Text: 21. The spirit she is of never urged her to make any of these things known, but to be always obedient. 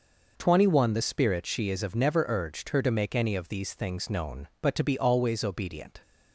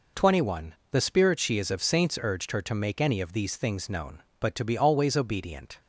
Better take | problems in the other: first | says "saints" for "never"; at 1.8 s

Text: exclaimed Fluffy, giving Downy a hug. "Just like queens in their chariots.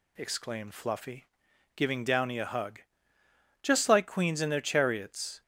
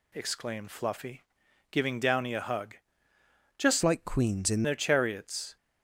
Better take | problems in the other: first | changes voice from "like" to "in"; from 3.8 to 4.6 s; 0.8 s long

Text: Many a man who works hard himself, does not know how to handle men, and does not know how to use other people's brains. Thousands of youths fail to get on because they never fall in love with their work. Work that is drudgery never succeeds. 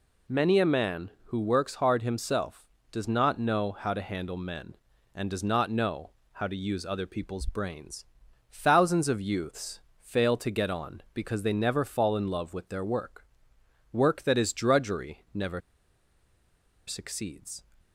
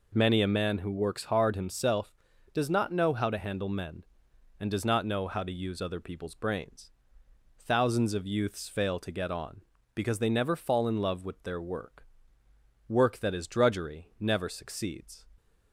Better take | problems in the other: second | pauses between "know" and "how"; slight; at 6.0 s; 0.24 s long // pauses between "youths" and "fail"; slight; at 9.8 s; 0.18 s long // pauses between "never" and "succeeds"; strong; at 15.6 s; 1.2 s long

